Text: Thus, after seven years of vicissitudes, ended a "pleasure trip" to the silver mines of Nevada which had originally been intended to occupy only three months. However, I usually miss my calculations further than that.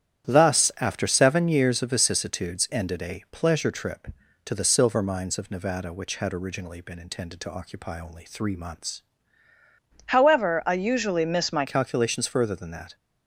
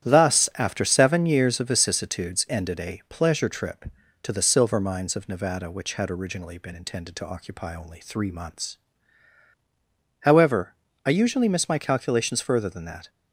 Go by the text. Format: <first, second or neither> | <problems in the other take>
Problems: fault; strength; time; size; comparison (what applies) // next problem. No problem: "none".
second | starts louder than the rest; strong; until 1.3 s; 10 dB; strong in the second // changes voice from "However" to "my"; from 10.0 to 11.6 s; 1.6 s long